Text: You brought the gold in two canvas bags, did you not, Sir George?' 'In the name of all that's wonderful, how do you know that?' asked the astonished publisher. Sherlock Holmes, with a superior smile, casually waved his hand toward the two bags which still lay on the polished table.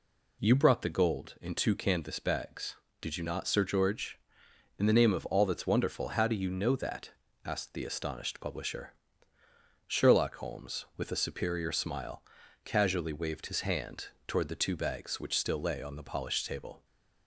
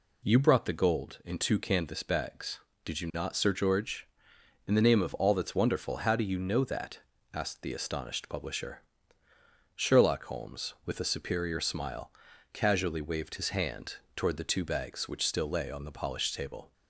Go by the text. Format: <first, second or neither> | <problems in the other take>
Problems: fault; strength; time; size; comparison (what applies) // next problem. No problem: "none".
neither | pauses between "hand" and "toward"; slight; the same in both